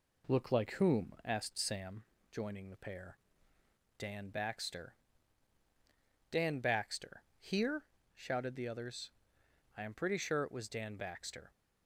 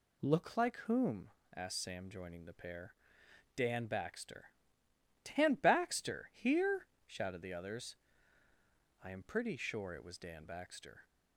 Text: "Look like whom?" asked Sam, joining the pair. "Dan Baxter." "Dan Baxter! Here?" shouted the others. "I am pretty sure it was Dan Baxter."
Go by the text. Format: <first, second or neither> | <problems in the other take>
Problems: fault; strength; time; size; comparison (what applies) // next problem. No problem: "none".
second | starts louder than the rest; slight; until 1.9 s; 3.5 dB